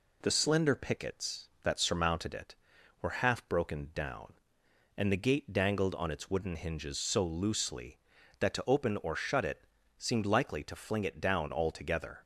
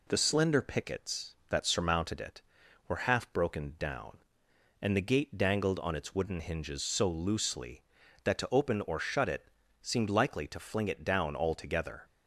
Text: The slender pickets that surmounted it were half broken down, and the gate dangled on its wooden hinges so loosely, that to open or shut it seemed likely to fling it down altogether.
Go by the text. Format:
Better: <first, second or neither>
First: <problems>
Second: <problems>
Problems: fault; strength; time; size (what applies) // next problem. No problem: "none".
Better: neither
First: pauses between "it" and "seemed"; slight; at 9.6 s; 0.34 s long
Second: pauses between "it" and "seemed"; slight; at 9.4 s; 0.34 s long